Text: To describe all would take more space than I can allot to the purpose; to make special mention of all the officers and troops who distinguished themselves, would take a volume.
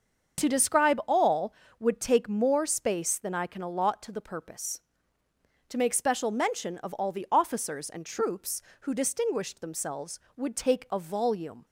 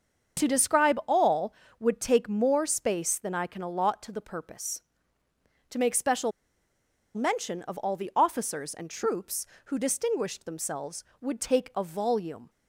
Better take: first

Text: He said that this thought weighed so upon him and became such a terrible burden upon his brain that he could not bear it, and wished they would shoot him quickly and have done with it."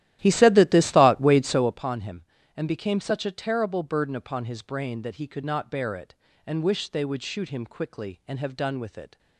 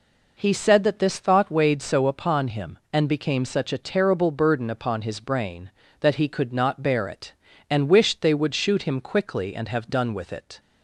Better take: second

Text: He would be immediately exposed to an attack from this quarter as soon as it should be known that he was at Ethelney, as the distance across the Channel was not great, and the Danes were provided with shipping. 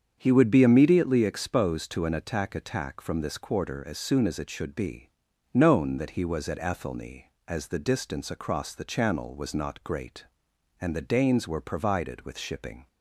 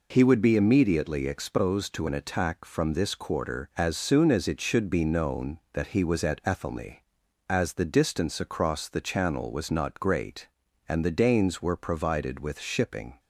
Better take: second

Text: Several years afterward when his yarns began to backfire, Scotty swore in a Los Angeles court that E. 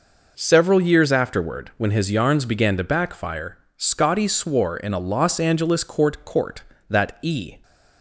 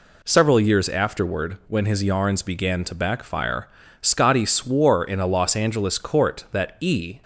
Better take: second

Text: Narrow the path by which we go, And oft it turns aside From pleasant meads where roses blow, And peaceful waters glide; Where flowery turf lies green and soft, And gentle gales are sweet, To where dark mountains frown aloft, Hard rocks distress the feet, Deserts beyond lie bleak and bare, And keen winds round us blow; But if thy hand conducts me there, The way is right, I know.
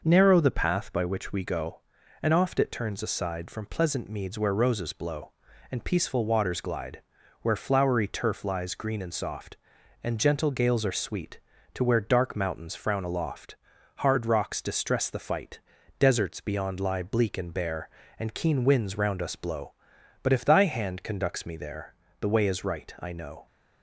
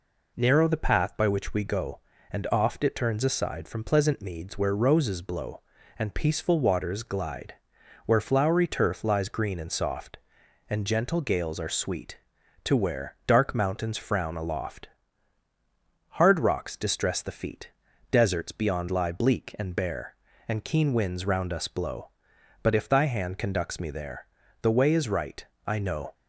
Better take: second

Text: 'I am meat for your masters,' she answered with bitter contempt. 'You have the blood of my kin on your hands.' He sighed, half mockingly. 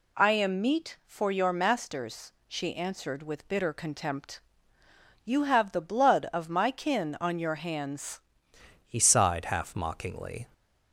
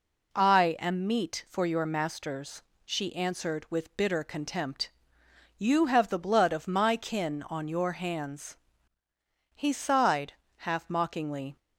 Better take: second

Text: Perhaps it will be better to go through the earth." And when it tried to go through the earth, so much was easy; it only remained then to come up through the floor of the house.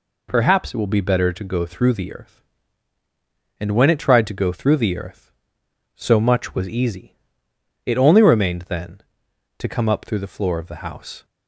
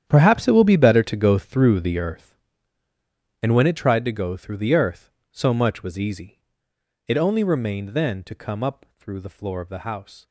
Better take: first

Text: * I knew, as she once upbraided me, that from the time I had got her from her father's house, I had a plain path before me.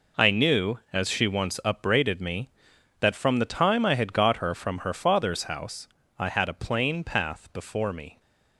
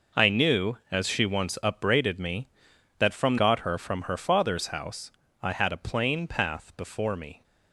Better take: first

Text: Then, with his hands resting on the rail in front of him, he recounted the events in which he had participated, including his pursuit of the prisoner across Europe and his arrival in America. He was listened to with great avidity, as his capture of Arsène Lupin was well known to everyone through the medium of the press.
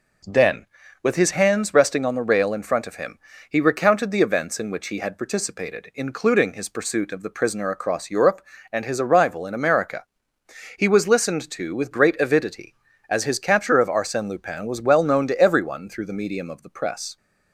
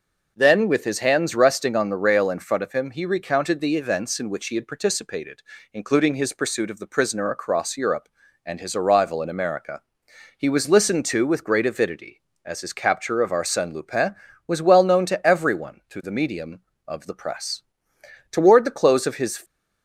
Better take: first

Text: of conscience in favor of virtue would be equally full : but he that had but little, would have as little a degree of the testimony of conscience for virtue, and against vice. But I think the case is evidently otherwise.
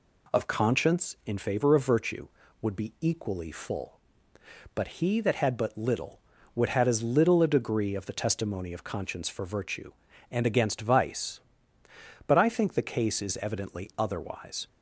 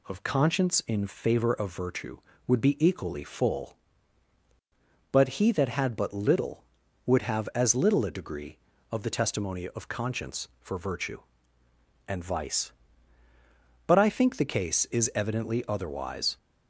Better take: first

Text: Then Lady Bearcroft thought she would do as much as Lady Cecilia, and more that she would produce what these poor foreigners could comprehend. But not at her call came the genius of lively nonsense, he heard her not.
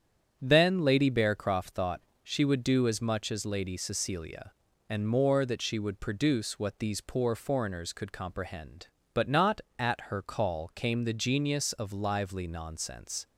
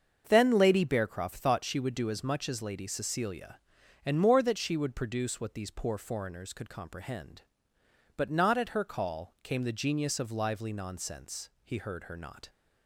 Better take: second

